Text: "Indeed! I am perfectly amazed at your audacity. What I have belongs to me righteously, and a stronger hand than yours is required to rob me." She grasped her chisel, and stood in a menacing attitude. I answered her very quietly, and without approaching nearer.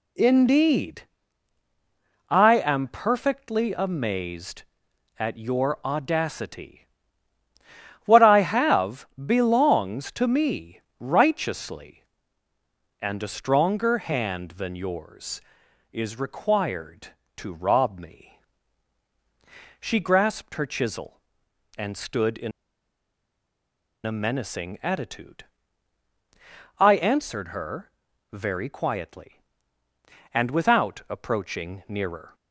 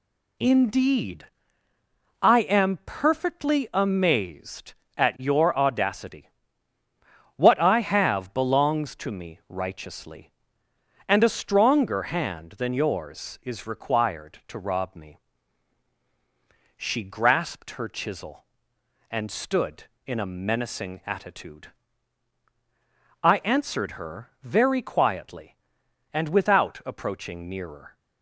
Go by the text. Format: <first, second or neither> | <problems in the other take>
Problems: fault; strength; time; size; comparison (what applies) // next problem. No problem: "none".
second | pauses between "have" and "belongs"; slight; at 9.0 s; 0.18 s long // pauses between "me" and "righteously"; slight; at 10.7 s; 0.18 s long // pauses between "in" and "a"; strong; at 22.5 s; 1.5 s long // pauses between "her" and "very"; at 27.9 s; 0.40 s long